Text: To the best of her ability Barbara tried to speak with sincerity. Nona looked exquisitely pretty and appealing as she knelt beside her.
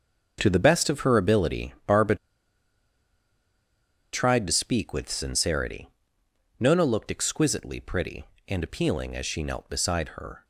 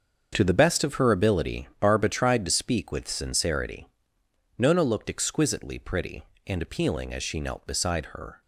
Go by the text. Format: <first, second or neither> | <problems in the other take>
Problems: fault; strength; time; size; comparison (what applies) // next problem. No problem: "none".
second | starts louder than the rest; until 1.4 s; 6.5 dB; also in the second // pauses between "Barbara" and "tried"; strong; at 2.1 s; 1.9 s long